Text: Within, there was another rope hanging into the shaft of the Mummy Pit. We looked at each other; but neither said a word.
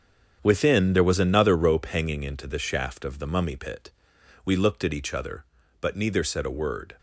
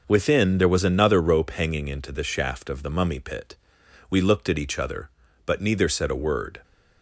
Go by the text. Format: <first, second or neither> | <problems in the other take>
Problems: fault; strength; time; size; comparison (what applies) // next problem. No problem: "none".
second | gets quieter; strong; throughout; 10 dB